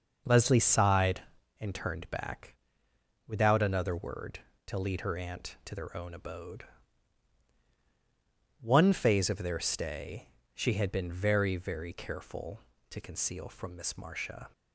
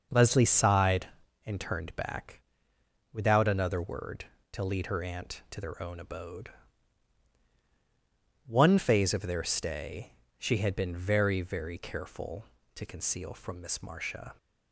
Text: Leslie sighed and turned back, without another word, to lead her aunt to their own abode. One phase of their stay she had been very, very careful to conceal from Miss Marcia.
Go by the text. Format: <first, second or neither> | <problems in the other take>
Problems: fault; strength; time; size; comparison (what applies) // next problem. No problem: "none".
neither | starts louder than the rest; noticeable; the same in both // pauses between "stay" and "she"; slight; the same in both